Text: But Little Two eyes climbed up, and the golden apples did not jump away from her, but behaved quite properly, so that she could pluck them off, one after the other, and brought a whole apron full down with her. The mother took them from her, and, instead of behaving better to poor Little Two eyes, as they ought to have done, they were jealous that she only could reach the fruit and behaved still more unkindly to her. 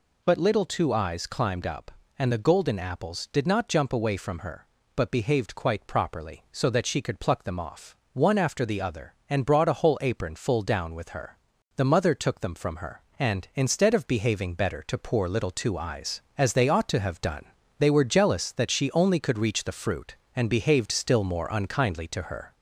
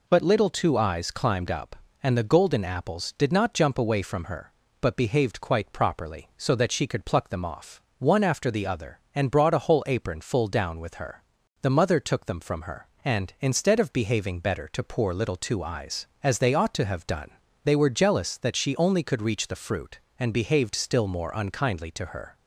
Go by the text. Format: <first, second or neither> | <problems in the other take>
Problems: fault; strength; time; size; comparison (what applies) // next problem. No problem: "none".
second | gets louder; slight; throughout; 2 dB